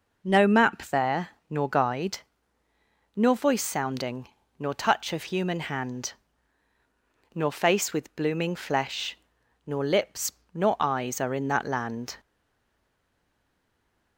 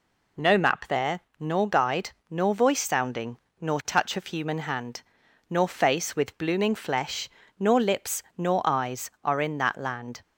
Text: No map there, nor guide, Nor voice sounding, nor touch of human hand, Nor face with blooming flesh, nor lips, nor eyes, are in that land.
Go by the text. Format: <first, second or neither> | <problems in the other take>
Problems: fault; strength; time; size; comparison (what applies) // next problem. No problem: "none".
second | stays silent after the last word; noticeable; from 12.1 s on; 2.0 s long